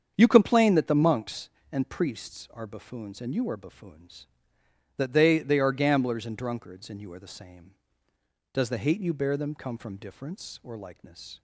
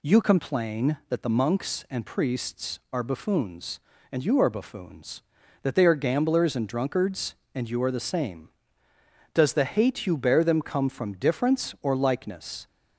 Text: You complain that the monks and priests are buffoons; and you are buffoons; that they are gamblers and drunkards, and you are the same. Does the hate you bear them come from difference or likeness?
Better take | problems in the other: second | starts louder than the rest; strong; until 1.1 s; 7.5 dB // says "they" twice; at 5.3 s

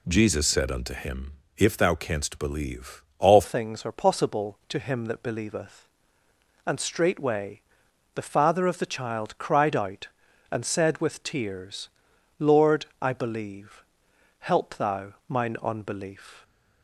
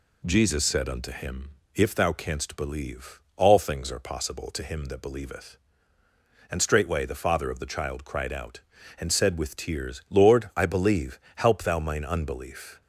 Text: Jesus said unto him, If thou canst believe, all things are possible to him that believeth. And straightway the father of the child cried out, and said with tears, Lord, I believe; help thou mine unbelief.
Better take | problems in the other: second | changes voice at "things"; from 3.4 s on; 13.0 s long // pauses between "straightway" and "the"; noticeable; at 7.6 s; 0.54 s long // pauses between "thou" and "mine"; slight; at 15.1 s; 0.16 s long

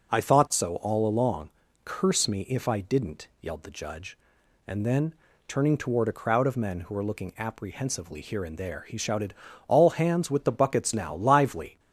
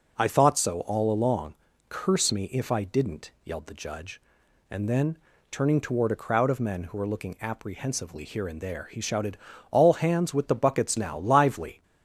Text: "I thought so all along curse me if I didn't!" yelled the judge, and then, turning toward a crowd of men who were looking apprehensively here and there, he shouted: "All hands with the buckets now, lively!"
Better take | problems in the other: neither | pauses between "along" and "curse"; slight; the same in both

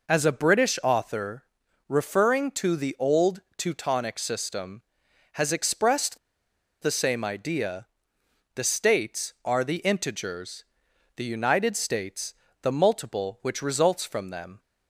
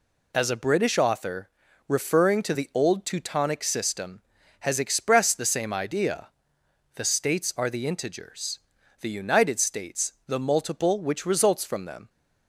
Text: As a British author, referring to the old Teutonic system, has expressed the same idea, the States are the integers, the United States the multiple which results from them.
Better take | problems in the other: second | pauses between "old" and "Teutonic"; slight; at 3.3 s; 0.16 s long // pauses between "expressed" and "the"; noticeable; at 6.1 s; 0.65 s long // pauses between "States" and "the"; slight; at 12.3 s; 0.30 s long

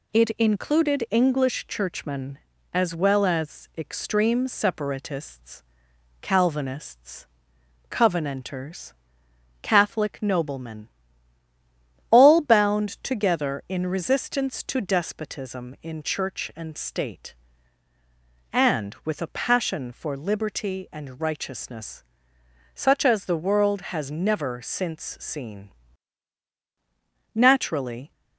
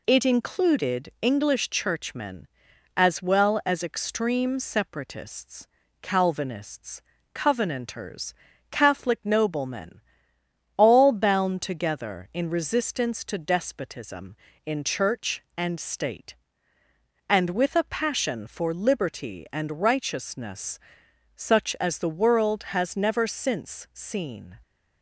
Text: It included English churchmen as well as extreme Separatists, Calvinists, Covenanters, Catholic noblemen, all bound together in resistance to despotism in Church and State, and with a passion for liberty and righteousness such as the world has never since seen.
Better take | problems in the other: second | pauses between "righteousness" and "such"; noticeable; at 22.0 s; 0.70 s long; noticeable in the second // goes on to say "Naturally"; noticeable; from 27.3 s on; 0.76 s long

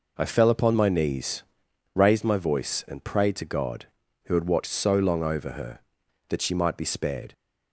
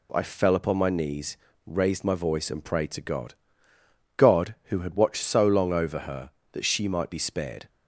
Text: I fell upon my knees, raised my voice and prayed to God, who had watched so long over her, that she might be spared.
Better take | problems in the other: first | says "God" twice; at 4.1 s

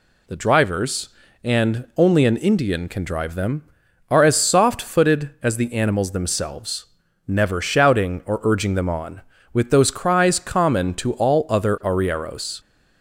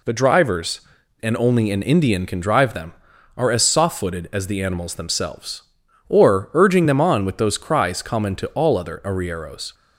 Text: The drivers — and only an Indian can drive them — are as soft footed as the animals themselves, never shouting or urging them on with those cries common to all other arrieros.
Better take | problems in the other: first | skips "never shouting"; at 5.8 s

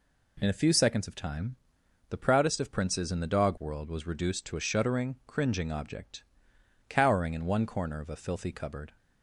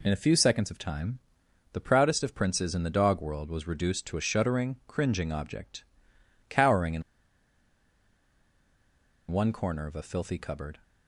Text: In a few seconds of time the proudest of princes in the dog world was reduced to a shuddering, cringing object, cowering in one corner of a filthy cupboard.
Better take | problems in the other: first | pauses between "time" and "the"; noticeable; at 1.1 s; 0.54 s long; noticeable in the first // pauses between "in" and "one"; strong; at 7.0 s; 2.2 s long

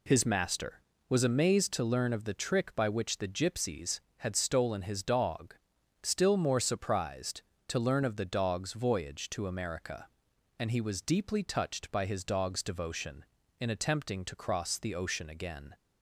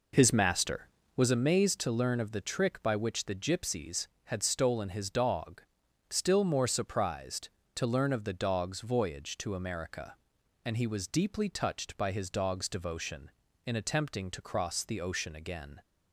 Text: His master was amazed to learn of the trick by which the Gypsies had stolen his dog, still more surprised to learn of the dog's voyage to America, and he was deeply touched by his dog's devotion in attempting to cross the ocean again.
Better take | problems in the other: first | starts louder than the rest; noticeable; until 1.3 s; 4.5 dB

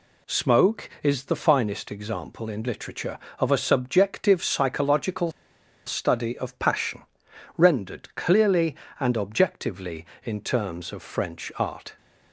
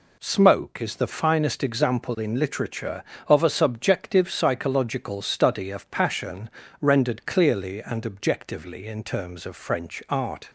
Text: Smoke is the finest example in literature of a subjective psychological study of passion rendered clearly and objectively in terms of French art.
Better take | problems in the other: second | pauses between "psychological" and "study"; noticeable; at 5.3 s; 0.54 s long // pauses between "passion" and "rendered"; noticeable; at 7.0 s; 0.54 s long; slight in the second

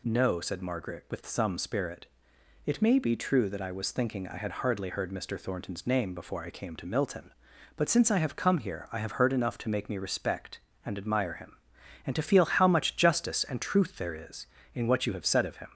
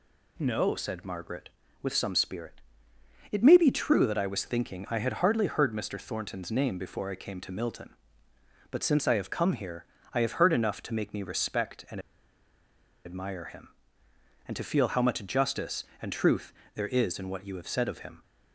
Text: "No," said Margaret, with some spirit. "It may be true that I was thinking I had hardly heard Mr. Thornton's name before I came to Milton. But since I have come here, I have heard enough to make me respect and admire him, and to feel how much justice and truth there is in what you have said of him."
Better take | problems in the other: first | pauses between "and" and "admire"; at 11.9 s; 1.0 s long // pauses between "truth" and "there"; slight; at 16.5 s; 0.22 s long

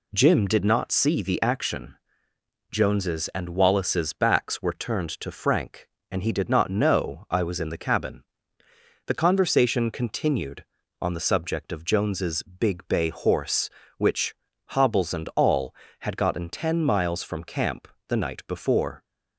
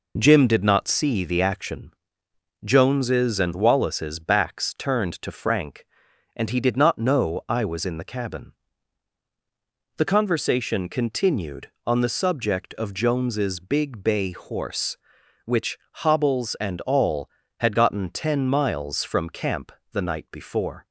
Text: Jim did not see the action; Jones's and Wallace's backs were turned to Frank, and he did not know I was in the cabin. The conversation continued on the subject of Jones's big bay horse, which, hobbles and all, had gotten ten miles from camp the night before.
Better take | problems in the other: first | skips "were"; at 4.7 s // pauses between "camp" and "the"; slight; at 19.7 s; 0.20 s long; slight in the first

